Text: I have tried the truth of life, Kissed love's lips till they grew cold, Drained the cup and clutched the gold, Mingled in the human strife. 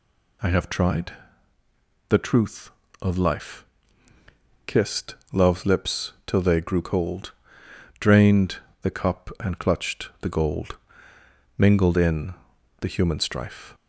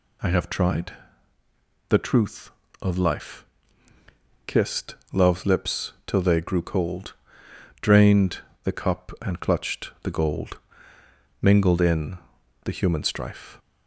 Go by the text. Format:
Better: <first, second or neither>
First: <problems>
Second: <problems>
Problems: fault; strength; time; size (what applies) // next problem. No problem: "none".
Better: neither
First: pauses between "tried" and "the"; noticeable; at 1.1 s; 0.98 s long // pauses between "Kissed" and "love's"; slight; at 5.1 s; 0.18 s long // pauses between "Drained" and "the"; slight; at 8.5 s; 0.24 s long // pauses between "in" and "the"; noticeable; at 12.3 s; 0.48 s long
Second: pauses between "tried" and "the"; noticeable; at 0.9 s; 0.98 s long // pauses between "Kissed" and "love's"; slight; at 4.9 s; 0.18 s long // pauses between "Drained" and "the"; slight; at 8.3 s; 0.24 s long // pauses between "in" and "the"; noticeable; at 12.1 s; 0.48 s long